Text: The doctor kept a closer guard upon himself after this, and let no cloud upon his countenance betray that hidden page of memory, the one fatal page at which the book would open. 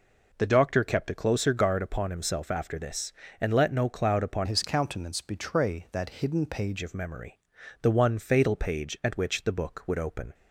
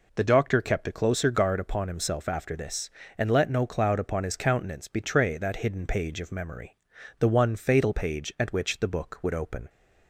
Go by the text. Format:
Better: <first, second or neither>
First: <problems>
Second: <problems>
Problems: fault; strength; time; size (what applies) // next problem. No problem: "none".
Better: second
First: changes voice from "his" to "page"; from 4.4 to 6.8 s; 2.4 s long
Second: none